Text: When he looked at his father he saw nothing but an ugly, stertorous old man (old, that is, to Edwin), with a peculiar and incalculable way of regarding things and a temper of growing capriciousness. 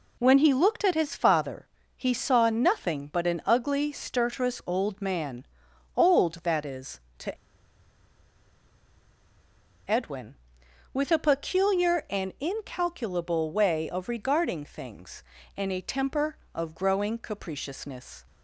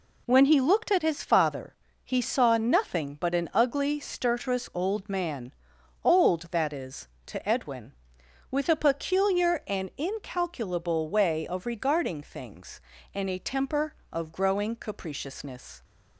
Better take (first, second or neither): second